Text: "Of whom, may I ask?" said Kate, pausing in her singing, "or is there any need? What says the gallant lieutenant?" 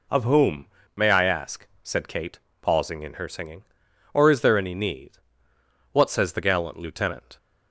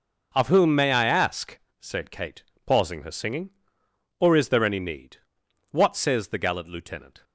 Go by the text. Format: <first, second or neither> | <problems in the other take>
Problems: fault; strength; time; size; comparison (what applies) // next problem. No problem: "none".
first | skips "in"; at 3.0 s